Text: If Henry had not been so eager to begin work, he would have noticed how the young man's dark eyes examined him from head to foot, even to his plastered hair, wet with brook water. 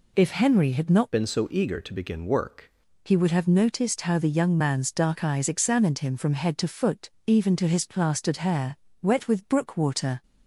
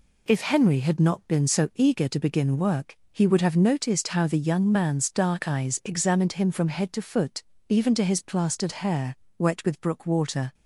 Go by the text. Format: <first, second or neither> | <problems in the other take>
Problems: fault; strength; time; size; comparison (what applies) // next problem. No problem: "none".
second | changes voice from "been" to "work"; from 1.1 to 2.6 s; 1.5 s long